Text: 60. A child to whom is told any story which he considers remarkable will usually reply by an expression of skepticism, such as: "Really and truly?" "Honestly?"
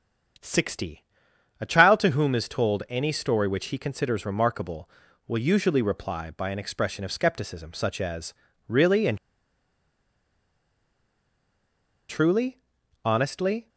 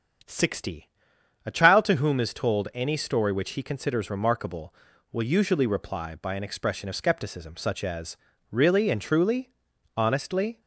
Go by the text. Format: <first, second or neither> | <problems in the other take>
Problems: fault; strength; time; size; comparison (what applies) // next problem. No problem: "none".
second | starts louder than the rest; strong; until 1.9 s; 8 dB; strong in the second // pauses between "and" and "truly"; strong; at 9.1 s; 2.9 s long